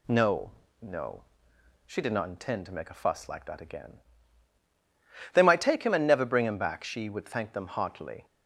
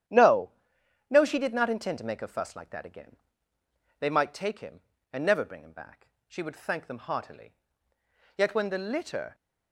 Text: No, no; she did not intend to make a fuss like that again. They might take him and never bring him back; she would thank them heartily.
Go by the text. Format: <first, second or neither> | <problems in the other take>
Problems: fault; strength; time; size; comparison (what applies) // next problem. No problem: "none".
first | starts louder than the rest; strong; until 1.6 s; 10 dB // goes on to say "Yet when the litter"; noticeable; from 8.3 s on; 0.98 s long